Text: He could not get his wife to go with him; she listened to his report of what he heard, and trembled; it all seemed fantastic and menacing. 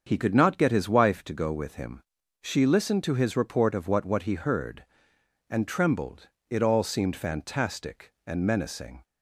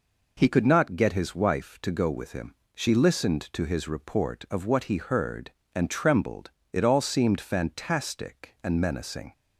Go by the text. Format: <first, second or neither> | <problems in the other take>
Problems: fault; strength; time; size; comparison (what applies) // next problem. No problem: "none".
second | starts louder than the rest; until 1.0 s; 7 dB // says "what" twice; at 4.0 s